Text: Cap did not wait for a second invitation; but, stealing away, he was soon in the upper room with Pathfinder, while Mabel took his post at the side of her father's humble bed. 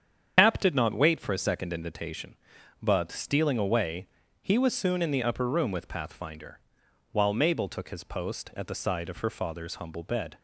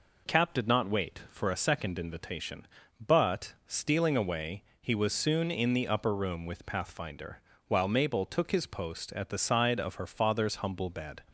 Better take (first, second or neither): second